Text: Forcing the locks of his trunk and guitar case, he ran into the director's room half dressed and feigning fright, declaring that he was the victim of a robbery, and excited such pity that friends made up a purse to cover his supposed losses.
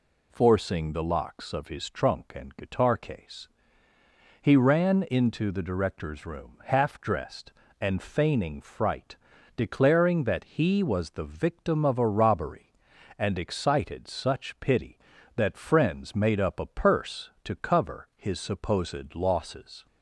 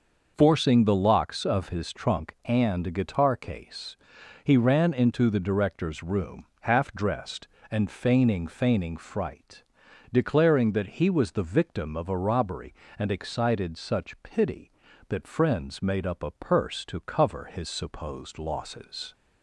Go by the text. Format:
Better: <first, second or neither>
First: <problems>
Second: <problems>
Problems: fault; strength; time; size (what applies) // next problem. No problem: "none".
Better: first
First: none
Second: starts louder than the rest; noticeable; until 1.3 s; 6 dB // pauses between "room" and "half"; slight; at 6.4 s; 0.16 s long // says "feigning" twice; at 8.4 s